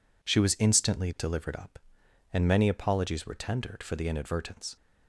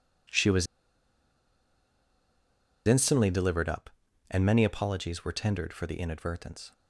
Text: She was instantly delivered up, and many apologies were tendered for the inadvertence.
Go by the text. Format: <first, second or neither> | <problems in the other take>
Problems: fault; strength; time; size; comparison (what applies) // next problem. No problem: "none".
first | pauses between "was" and "instantly"; strong; at 0.6 s; 2.2 s long